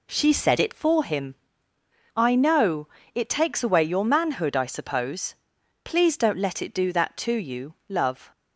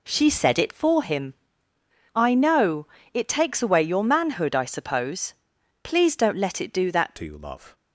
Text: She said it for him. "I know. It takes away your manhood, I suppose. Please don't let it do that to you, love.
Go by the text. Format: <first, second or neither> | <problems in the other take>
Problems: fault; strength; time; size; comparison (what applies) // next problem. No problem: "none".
first | changes voice at "to"; from 7.1 s on; 0.6 s long